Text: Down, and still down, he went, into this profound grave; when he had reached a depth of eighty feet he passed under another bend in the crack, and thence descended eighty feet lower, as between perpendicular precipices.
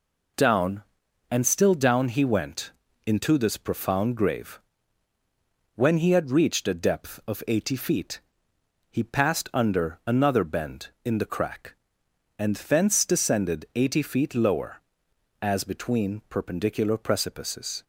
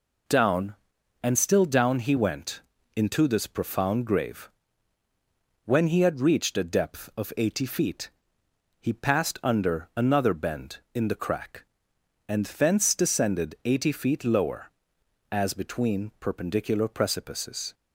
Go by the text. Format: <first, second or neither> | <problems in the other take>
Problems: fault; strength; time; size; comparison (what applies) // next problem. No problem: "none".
neither | pauses between "feet" and "he"; noticeable; the same in both